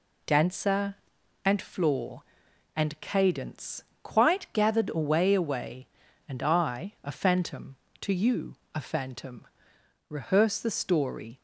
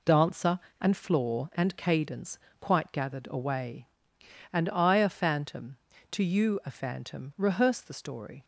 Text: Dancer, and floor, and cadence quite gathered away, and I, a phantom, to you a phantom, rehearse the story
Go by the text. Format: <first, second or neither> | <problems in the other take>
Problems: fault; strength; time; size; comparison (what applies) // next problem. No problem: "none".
second | pauses between "cadence" and "quite"; slight; at 3.8 s; 0.22 s long; slight in the second // says "away" twice; at 5.3 s // pauses between "you" and "a"; slight; at 8.5 s; 0.18 s long